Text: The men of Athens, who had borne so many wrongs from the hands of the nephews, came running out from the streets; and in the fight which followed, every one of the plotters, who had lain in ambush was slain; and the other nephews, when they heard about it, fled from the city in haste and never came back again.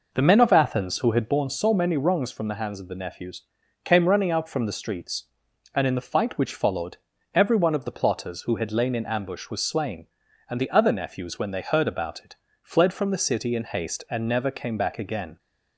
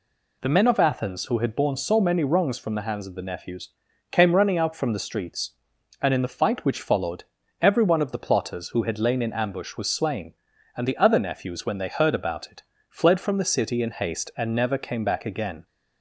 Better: second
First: starts louder than the rest; noticeable; until 1.4 s; 5 dB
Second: none

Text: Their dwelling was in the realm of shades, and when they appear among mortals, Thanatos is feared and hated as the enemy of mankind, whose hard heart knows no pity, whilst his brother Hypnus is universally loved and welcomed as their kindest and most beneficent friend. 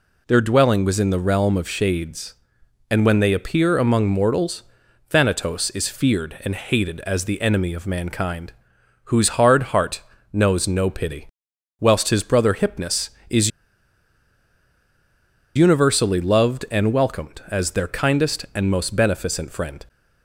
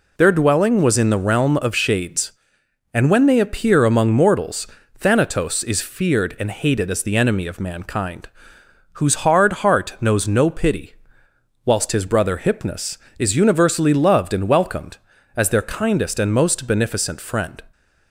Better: second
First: pauses between "heart" and "knows"; slight; at 9.9 s; 0.32 s long // pauses between "is" and "universally"; strong; at 13.5 s; 2.0 s long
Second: none

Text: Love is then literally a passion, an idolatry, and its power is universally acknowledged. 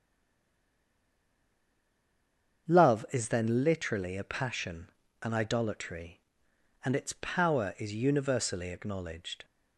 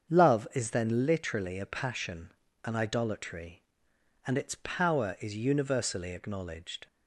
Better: second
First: stays silent before the first word; strong; until 2.6 s; 2.6 s long // starts louder than the rest; until 3.7 s; 7 dB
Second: starts louder than the rest; until 1.1 s; 7 dB

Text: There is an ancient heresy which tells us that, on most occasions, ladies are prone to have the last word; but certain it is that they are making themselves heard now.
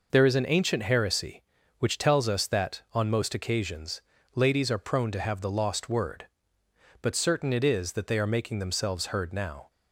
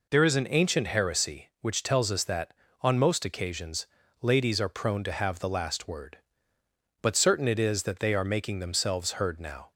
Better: second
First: says "lost" for "last"; at 5.4 s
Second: none

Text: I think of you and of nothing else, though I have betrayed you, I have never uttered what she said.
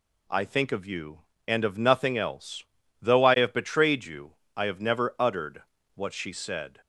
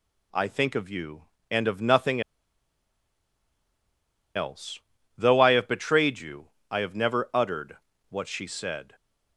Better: first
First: pauses between "uttered" and "what"; slight; at 5.6 s; 0.32 s long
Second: pauses between "nothing" and "else"; strong; at 2.2 s; 2.1 s long // pauses between "uttered" and "what"; slight; at 7.7 s; 0.32 s long

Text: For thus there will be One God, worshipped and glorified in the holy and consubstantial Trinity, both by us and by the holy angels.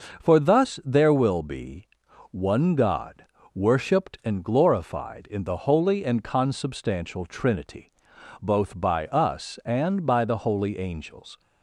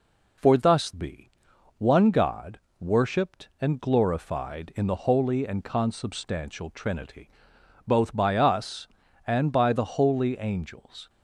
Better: first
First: pauses between "be" and "One"; noticeable; at 1.8 s; 0.46 s long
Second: skips "there will"; at 0.9 s // pauses between "be" and "One"; noticeable; at 1.3 s; 0.46 s long

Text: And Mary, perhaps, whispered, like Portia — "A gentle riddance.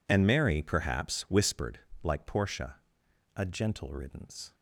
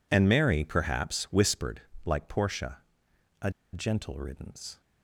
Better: first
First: none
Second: pauses between "A" and "gentle"; slight; at 3.4 s; 0.23 s long

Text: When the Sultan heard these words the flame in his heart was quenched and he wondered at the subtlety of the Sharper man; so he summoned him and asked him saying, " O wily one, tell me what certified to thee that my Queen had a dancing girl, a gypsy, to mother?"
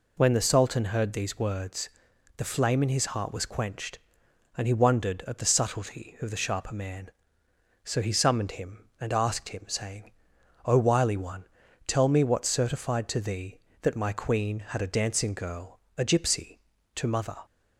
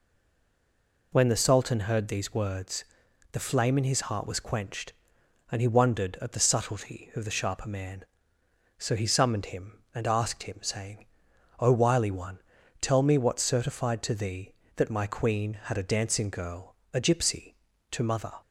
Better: first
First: pauses between "words" and "the"; noticeable; at 1.8 s; 0.48 s long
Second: stays silent before the first word; until 1.1 s; 1.1 s long // pauses between "words" and "the"; noticeable; at 2.8 s; 0.48 s long

